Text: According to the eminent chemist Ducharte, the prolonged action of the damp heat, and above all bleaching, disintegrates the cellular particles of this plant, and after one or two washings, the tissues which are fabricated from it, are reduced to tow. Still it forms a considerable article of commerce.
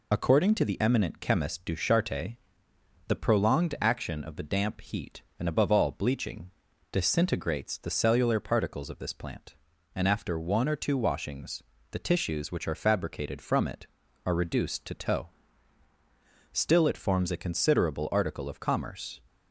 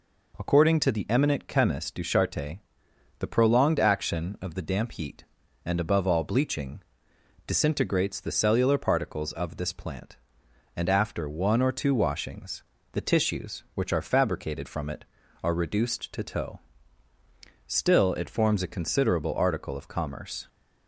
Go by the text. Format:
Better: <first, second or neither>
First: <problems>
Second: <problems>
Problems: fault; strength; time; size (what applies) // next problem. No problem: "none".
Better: second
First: loses the start of "According"; at 0.1 s; 35 ms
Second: none